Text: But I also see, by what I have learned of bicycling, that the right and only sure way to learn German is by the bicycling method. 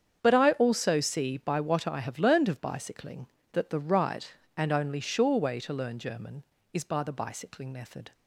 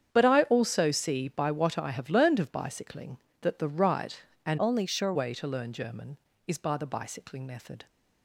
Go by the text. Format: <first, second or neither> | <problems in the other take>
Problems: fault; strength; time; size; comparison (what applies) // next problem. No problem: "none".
first | starts louder than the rest; strong; until 1.1 s; 8 dB; strong in the first // changes voice from "only" to "sure"; from 4.5 to 5.1 s; 0.6 s long